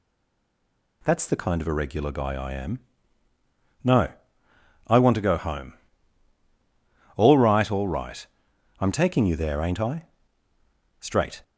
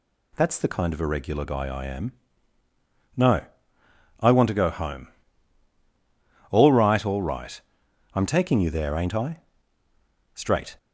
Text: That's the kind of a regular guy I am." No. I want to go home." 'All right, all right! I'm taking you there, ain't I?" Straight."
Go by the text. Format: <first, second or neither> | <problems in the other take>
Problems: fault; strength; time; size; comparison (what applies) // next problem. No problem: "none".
second | stays silent before the first word; until 1.0 s; 1.0 s long